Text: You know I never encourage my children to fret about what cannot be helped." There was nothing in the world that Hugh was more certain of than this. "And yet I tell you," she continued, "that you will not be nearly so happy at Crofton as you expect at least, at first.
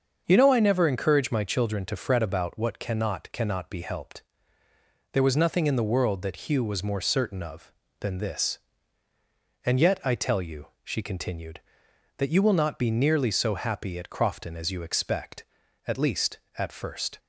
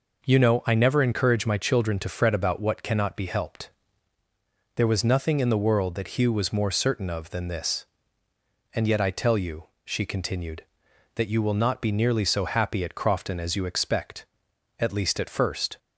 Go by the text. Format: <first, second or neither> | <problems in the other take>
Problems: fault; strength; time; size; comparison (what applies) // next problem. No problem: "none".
second | starts louder than the rest; until 1.2 s; 6.5 dB // says "cannot" twice; at 3.3 s